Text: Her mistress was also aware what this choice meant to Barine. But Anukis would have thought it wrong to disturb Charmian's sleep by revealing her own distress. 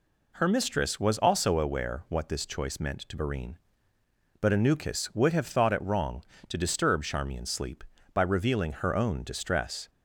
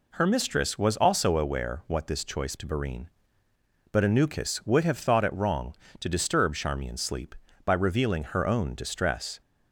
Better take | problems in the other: first | skips "meant"; at 2.5 s

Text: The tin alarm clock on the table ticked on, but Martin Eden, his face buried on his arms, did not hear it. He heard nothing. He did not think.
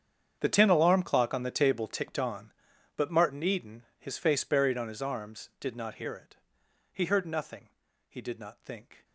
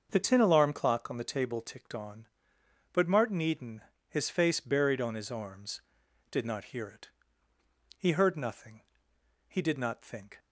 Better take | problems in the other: second | gets quieter; strong; throughout; 18 dB // starts louder than the rest; strong; until 1.4 s; 8 dB; also in the second

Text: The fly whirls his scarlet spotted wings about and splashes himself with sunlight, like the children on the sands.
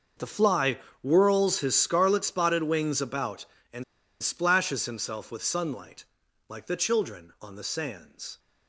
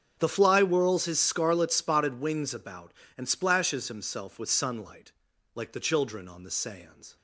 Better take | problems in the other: second | starts louder than the rest; until 1.4 s; 6 dB; strong in the second // pauses between "fly" and "whirls"; slight; at 0.7 s; 0.24 s long // pauses between "and" and "splashes"; at 3.8 s; 0.38 s long

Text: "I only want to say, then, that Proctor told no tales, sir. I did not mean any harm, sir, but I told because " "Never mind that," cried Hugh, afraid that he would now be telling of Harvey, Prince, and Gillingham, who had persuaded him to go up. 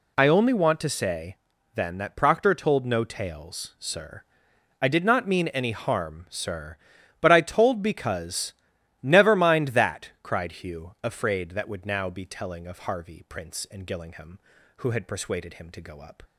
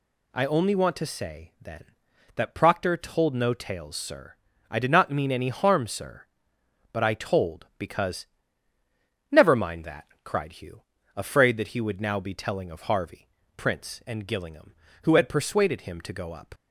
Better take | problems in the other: second | skips "he"; at 11.6 s

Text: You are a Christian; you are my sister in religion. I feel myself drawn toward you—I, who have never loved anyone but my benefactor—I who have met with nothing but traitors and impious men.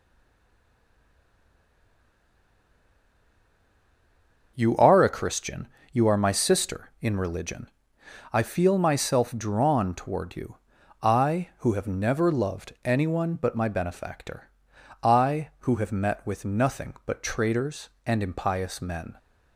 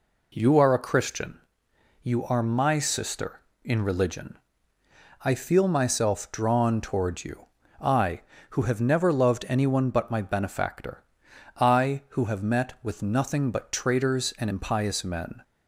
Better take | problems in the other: second | stays silent before the first word; strong; until 4.5 s; 4.5 s long // starts louder than the rest; noticeable; until 5.5 s; 6 dB

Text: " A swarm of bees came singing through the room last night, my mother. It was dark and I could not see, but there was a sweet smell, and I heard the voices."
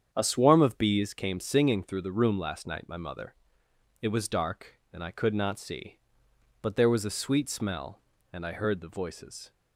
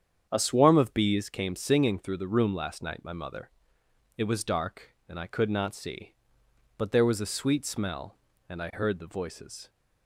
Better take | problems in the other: neither | starts louder than the rest; strong; the same in both

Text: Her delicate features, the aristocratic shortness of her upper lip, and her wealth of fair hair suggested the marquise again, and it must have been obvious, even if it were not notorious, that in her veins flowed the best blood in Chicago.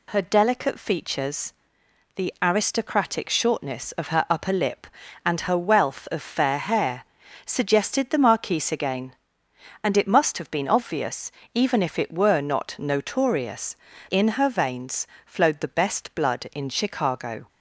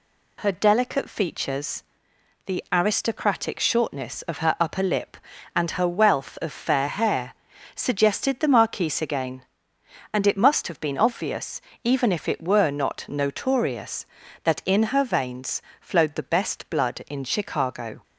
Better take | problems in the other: second | pauses between "hair" and "suggested"; at 7.0 s; 0.40 s long; also in the second // skips "that"; at 13.9 s // pauses between "veins" and "flowed"; slight; at 15.0 s; 0.20 s long; slight in the second

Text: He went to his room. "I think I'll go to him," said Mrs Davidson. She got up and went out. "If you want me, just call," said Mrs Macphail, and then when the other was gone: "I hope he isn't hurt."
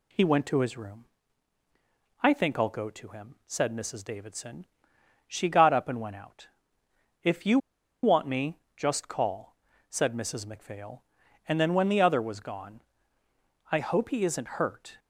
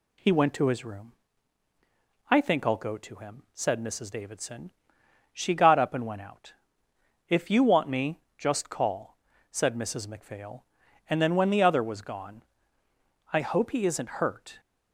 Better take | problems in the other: second | pauses between "you" and "want"; at 7.5 s; 0.45 s long

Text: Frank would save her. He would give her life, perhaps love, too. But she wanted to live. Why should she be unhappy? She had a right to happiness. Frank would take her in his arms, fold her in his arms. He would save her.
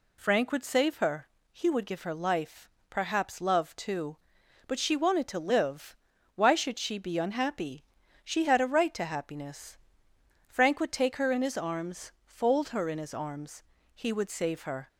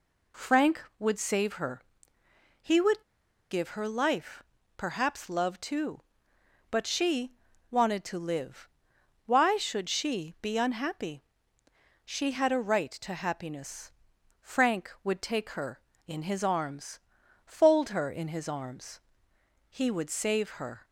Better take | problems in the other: first | pauses between "would" and "give"; noticeable; at 3.0 s; 0.49 s long // pauses between "she" and "wanted"; at 7.3 s; 0.40 s long

